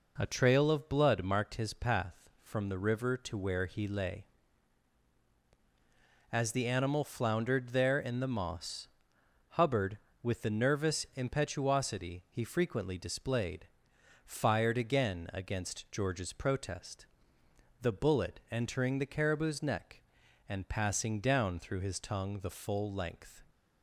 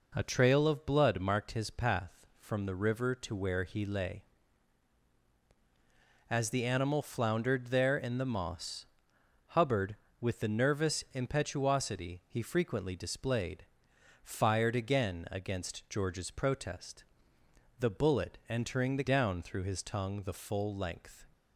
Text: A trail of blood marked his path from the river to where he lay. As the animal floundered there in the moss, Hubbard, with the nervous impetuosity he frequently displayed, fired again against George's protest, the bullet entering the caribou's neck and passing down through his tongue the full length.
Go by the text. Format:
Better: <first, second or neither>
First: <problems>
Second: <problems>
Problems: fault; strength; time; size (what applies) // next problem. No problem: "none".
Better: first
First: none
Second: skips "caribou's neck and passing"; at 19.0 s